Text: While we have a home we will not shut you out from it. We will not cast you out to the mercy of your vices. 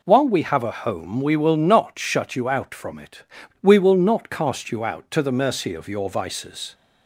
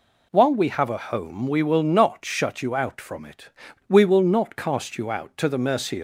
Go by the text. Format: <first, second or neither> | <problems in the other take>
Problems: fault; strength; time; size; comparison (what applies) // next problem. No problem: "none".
first | stops before "of your vices"; at 5.9 s